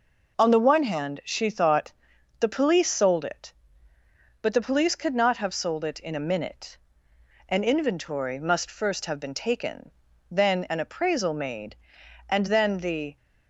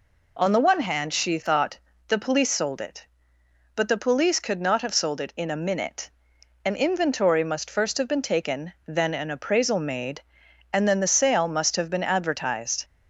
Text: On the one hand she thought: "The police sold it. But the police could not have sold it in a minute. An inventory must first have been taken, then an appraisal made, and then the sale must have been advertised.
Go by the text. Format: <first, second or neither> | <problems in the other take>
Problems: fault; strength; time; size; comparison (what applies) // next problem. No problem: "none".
second | stops before "sale must have been advertised"; at 13.1 s